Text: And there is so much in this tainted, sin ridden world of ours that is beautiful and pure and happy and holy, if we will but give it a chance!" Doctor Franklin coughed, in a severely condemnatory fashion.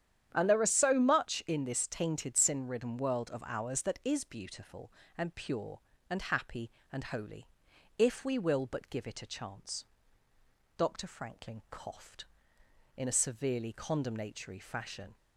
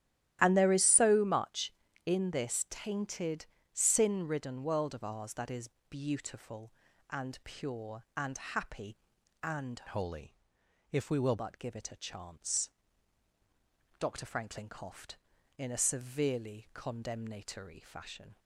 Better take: first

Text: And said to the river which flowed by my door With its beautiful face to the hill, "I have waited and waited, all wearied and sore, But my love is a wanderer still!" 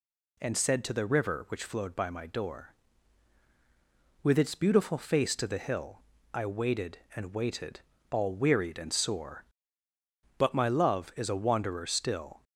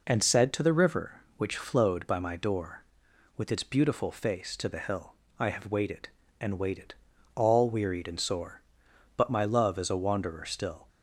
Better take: second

